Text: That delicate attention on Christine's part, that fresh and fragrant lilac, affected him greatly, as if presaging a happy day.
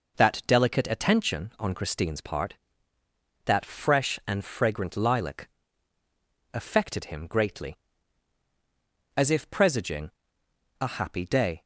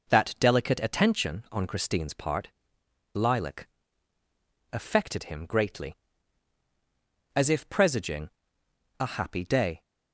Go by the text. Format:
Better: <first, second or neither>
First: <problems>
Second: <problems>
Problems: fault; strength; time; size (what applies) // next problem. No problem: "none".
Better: first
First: pauses between "presaging" and "a"; noticeable; at 10.1 s; 0.68 s long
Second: skips "that fresh and fragrant"; at 2.8 s // pauses between "presaging" and "a"; noticeable; at 8.2 s; 0.68 s long